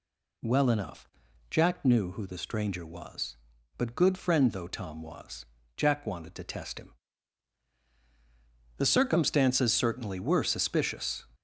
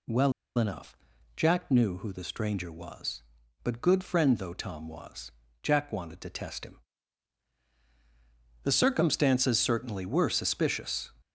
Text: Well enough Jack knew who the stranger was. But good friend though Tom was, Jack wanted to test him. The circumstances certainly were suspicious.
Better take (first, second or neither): first